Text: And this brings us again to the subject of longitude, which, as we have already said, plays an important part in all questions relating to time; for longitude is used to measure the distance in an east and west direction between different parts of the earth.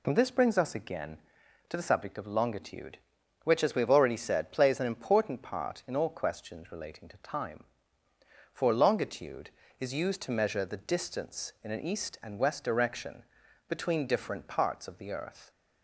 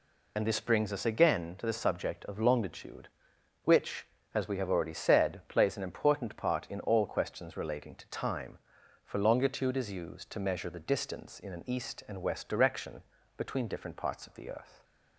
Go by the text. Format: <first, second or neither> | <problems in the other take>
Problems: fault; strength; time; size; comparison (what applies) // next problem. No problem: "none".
first | loses the start of "And"; at 0.3 s; 65 ms // pauses between "direction" and "between"; slight; at 13.0 s; 0.34 s long; also in the first